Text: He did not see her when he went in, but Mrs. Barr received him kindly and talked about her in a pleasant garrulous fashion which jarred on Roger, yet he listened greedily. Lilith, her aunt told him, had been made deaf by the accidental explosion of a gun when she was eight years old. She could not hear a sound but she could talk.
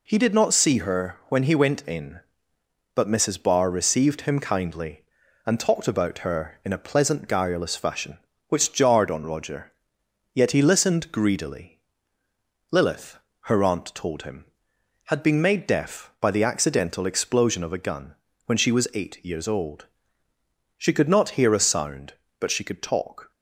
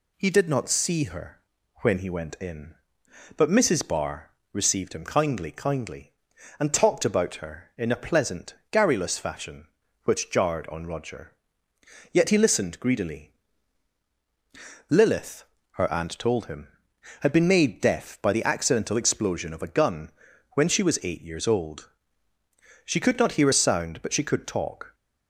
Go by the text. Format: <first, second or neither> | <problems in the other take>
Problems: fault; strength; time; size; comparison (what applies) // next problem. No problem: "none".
first | pauses between "her" and "when"; at 1.3 s; 0.42 s long // pauses between "Barr" and "received"; slight; at 4.2 s; 0.22 s long // says "kindly" twice; at 5.4 s // pauses between "pleasant" and "garrulous"; slight; at 8.5 s; 0.16 s long // pauses between "gun" and "when"; at 20.0 s; 0.44 s long; slight in the first